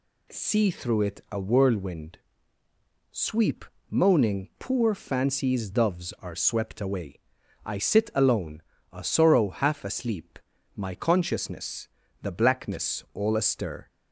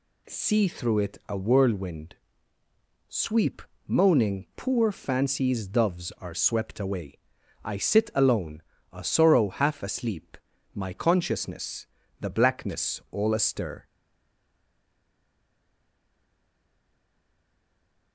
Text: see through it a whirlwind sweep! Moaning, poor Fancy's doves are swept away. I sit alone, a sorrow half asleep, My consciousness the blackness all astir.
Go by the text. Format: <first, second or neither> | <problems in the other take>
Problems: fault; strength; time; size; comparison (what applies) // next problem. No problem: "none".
first | pauses between "whirlwind" and "sweep"; noticeable; at 2.1 s; 0.94 s long; noticeable in the first // pauses between "consciousness" and "the"; slight; at 11.8 s; 0.32 s long; slight in the first // stays silent after the last word; strong; from 13.8 s on; 4.3 s long